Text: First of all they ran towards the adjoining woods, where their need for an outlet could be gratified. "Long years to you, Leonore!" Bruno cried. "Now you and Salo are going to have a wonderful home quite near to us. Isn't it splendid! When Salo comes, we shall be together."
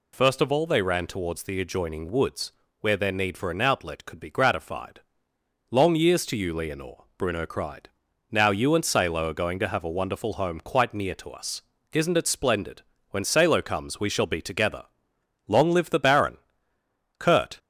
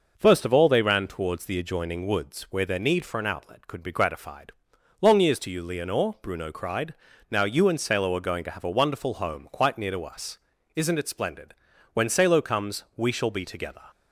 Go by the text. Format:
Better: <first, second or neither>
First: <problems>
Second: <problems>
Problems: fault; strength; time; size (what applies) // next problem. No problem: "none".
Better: second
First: goes on to say "Long live the Baron Kurt"; strong; from 15.4 s on; 2.1 s long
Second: none